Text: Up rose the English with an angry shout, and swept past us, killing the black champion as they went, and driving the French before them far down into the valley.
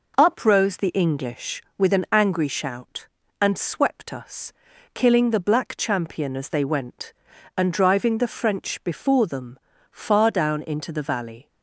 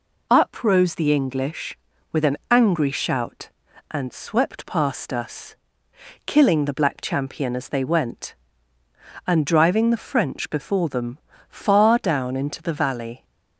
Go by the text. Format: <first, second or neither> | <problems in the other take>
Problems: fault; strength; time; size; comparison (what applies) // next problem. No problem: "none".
second | skips "past"; at 4.1 s // pauses between "them" and "far"; slight; at 9.5 s; 0.32 s long; slight in the second